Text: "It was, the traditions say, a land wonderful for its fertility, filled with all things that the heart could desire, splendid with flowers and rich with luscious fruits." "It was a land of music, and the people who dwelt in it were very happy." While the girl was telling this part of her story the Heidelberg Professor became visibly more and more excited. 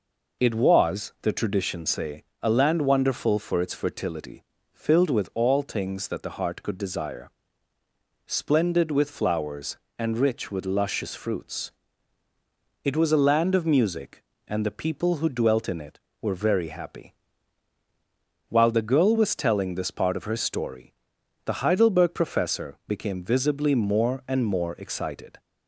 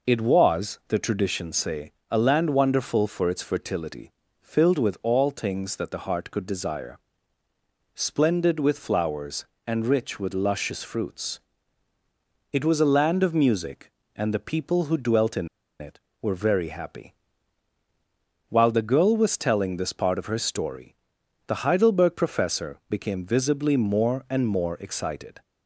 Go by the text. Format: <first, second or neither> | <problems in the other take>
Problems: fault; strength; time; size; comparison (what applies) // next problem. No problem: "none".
first | pauses between "in" and "it"; slight; at 15.4 s; 0.32 s long // pauses between "story" and "the"; noticeable; at 20.9 s; 0.50 s long; noticeable in the first